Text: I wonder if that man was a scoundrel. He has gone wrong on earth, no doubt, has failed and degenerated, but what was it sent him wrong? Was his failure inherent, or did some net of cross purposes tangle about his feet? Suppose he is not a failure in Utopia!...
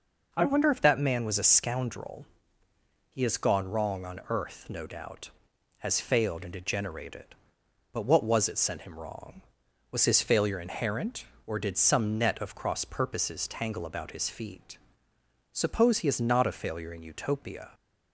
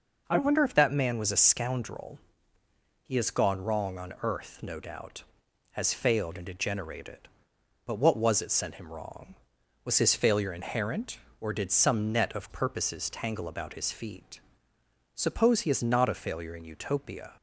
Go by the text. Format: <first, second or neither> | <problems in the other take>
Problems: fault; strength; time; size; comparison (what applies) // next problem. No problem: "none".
first | skips "cross"; at 12.4 s